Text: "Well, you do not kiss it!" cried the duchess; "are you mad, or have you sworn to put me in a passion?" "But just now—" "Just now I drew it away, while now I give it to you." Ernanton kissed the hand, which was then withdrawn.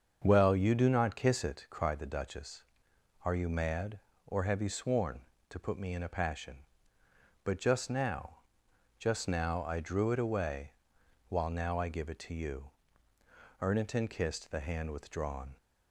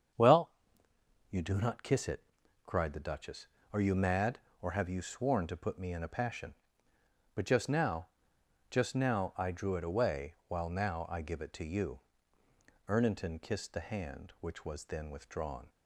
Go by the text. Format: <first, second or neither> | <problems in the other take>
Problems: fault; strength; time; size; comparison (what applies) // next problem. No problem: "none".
second | starts louder than the rest; until 1.2 s; 7 dB; strong in the second // skips "which was then"; at 14.9 s